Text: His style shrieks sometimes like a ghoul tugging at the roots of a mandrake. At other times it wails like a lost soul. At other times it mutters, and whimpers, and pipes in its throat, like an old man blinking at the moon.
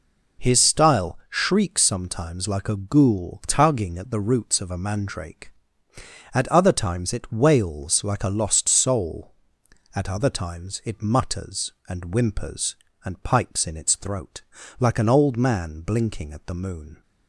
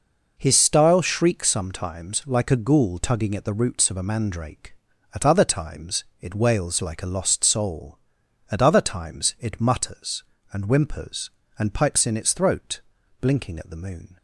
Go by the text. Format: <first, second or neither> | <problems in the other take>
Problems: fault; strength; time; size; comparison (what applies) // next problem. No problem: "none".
first | pauses between "times" and "it"; slight; at 6.0 s; 0.18 s long // skips "like an old man"; at 13.0 s